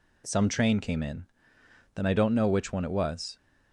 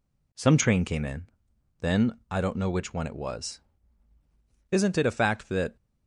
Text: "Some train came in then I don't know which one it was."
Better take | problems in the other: first | pauses between "in" and "then"; noticeable; at 1.2 s; 0.56 s long; noticeable in the first // goes on to say "Isn't it a fact that"; noticeable; from 4.6 s on; 1.0 s long

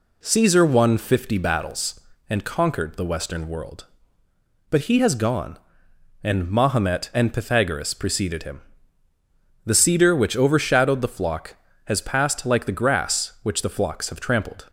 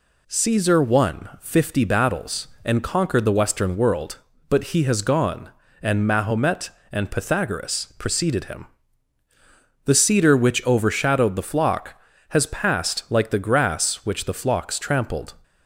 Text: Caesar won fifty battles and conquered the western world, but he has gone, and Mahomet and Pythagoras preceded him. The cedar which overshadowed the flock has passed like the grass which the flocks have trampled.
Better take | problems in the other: first | skips "have"; at 14.7 s

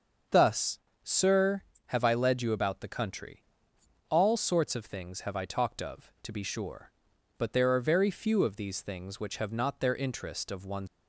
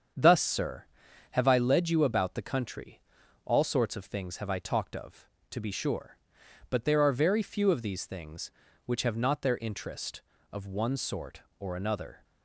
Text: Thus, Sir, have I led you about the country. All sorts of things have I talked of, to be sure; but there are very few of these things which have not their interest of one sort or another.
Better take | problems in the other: second | starts louder than the rest; until 1.5 s; 6.5 dB; strong in the second // stops before "sort or another"; at 10.8 s

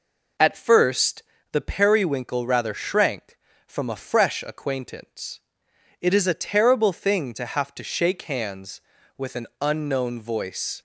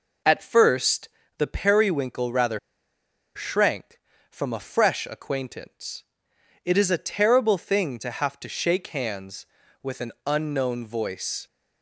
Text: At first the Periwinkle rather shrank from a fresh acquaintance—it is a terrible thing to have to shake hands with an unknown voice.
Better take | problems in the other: first | pauses between "first" and "the"; slight; at 1.0 s; 0.30 s long; slight in the first // pauses between "rather" and "shrank"; noticeable; at 2.5 s; 0.76 s long // pauses between "an" and "unknown"; slight; at 10.1 s; 0.16 s long; slight in the first

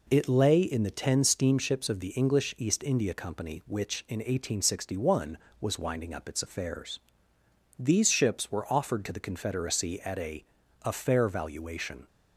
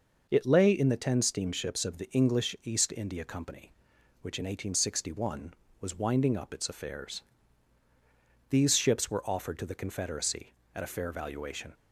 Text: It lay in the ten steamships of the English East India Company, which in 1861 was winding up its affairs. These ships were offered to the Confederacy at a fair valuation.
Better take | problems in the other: second | says "a" twice; at 10.8 s

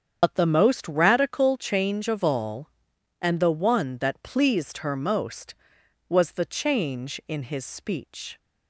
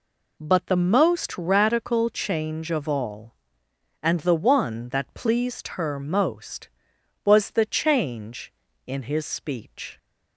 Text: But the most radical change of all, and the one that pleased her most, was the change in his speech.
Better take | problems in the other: second | loses the start of "But"; at 0.2 s; 75 ms // starts louder than the rest; strong; until 1.2 s; 7.5 dB

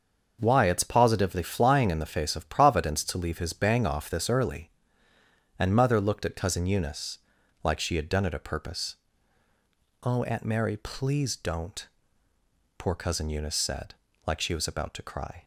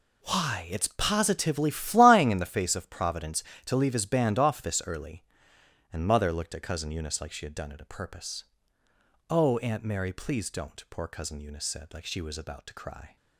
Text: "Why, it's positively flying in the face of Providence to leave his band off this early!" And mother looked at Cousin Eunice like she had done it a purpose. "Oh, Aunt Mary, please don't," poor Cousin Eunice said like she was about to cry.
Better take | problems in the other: second | starts louder than the rest; until 1.4 s; 6.5 dB // says "bang" for "band"; at 3.5 s // pauses between "Eunice" and "like"; at 7.1 s; 0.44 s long // pauses between "said" and "like"; slight; at 13.9 s; 0.30 s long

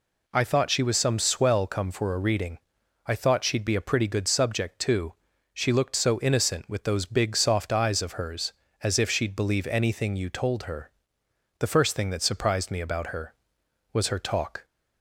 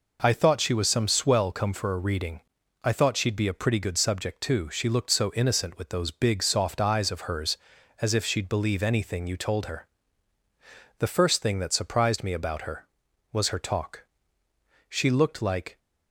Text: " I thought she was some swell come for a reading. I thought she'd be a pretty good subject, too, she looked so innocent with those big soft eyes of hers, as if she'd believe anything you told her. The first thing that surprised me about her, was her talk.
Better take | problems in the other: first | goes on to say "She looked like"; noticeable; from 14.8 s on; 0.88 s long

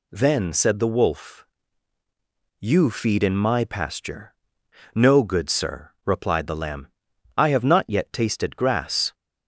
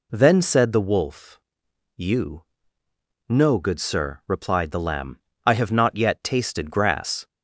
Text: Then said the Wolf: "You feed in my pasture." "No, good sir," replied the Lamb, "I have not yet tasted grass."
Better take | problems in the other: first | skips "feed in my pasture"; at 2.8 s

